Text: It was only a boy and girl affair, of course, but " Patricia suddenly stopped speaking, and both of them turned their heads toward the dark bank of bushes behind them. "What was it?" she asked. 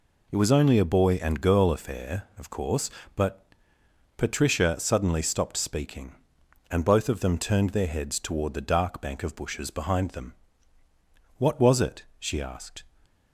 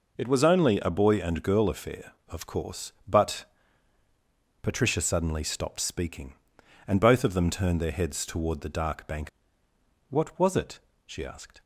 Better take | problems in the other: first | skips "of bushes behind them"; at 9.6 s

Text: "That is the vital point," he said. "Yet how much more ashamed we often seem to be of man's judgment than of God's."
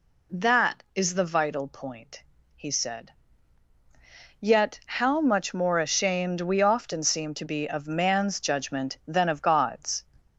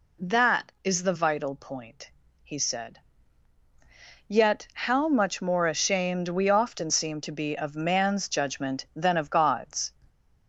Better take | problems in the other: neither | none

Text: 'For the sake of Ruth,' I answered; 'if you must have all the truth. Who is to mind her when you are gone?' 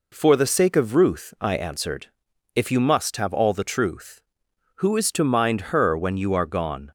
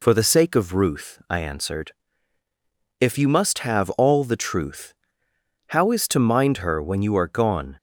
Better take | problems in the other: first | says "How" for "Who"; at 5.6 s

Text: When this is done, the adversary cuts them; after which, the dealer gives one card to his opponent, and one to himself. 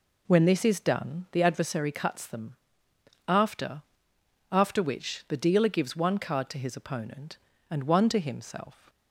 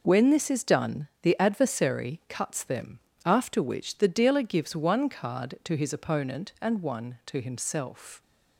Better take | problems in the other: second | says "after" twice; at 4.5 s

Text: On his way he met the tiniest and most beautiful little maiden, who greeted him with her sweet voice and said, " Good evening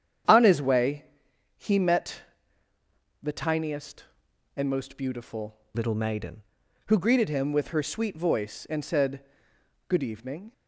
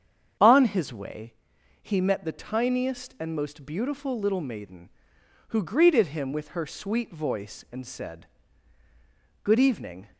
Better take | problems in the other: second | starts louder than the rest; strong; until 1.8 s; 9 dB; strong in the second // pauses between "way" and "he"; noticeable; at 1.0 s; 0.52 s long; noticeable in the second // pauses between "met" and "the"; at 2.2 s; 1.0 s long // changes voice from "little" to "maiden"; from 5.7 to 6.4 s; 0.7 s long

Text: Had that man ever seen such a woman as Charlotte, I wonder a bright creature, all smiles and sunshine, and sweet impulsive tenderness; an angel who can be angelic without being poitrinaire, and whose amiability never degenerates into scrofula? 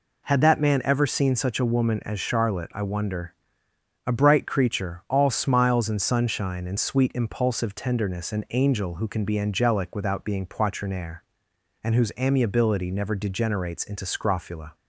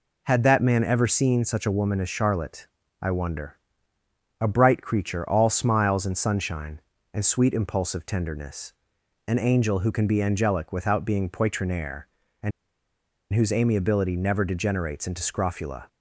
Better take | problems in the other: first | pauses between "wonder" and "a"; noticeable; at 3.5 s; 0.82 s long; noticeable in the first // pauses between "and" and "whose"; noticeable; at 12.5 s; 0.82 s long

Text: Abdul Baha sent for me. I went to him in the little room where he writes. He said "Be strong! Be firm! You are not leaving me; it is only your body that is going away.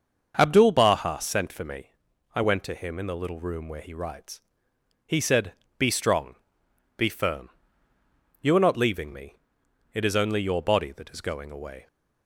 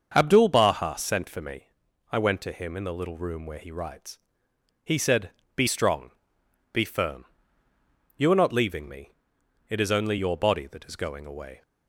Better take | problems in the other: neither | starts louder than the rest; the same in both // pauses between "said" and "Be"; slight; the same in both

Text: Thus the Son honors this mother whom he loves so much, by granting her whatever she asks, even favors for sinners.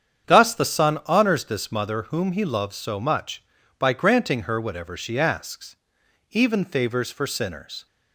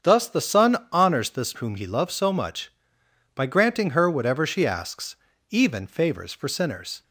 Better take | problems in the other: first | starts louder than the rest; strong; until 1.1 s; 7.5 dB; strong in the first // pauses between "Son" and "honors"; slight; at 0.7 s; 0.16 s long // skips "mother"; at 1.5 s

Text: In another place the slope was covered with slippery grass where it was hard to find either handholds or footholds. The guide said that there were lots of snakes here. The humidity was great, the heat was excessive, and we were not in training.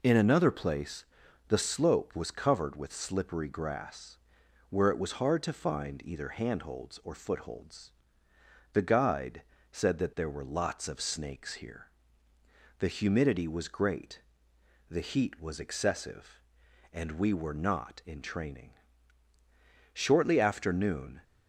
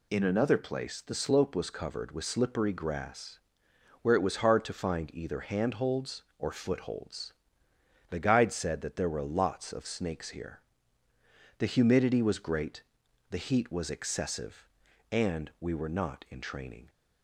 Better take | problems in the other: second | pauses between "place" and "the"; at 1.0 s; 0.44 s long // pauses between "grass" and "where"; noticeable; at 4.1 s; 0.54 s long; noticeable in the second // pauses between "guide" and "said"; slight; at 9.4 s; 0.30 s long // goes on to say "Shortly after noon"; noticeable; from 19.9 s on; 1.3 s long

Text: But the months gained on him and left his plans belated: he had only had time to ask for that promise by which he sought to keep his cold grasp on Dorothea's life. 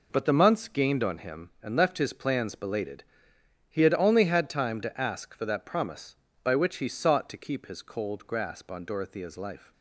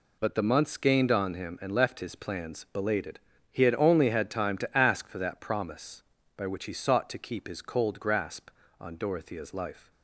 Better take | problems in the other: neither | none

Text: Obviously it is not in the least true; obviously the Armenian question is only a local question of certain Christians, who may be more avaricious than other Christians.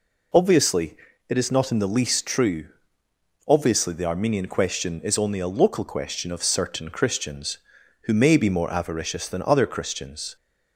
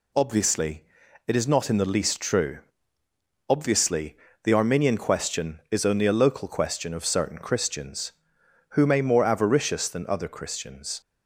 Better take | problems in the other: first | pauses between "Obviously" and "it"; at 0.8 s; 0.42 s long; slight in the first // pauses between "obviously" and "the"; slight; at 4.1 s; 0.30 s long // skips "be"; at 9.0 s

